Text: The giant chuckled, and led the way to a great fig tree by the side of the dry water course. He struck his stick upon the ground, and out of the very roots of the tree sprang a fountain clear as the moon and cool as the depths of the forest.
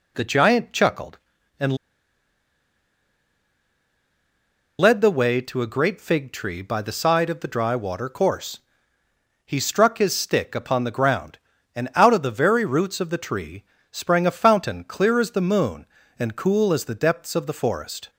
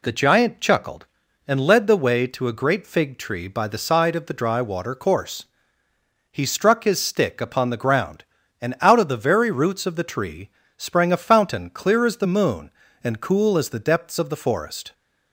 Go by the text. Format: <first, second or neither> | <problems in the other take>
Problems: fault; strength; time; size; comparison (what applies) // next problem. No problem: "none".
second | pauses between "and" and "led"; strong; at 1.7 s; 3.0 s long // pauses between "tree" and "sprang"; slight; at 13.6 s; 0.26 s long; slight in the second